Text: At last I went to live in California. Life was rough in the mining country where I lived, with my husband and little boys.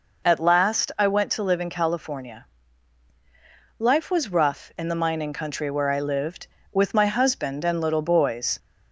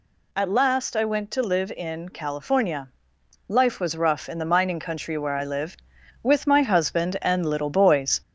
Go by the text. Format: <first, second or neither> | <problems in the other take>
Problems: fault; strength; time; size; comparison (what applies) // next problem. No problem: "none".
first | gets louder; slight; throughout; 2.5 dB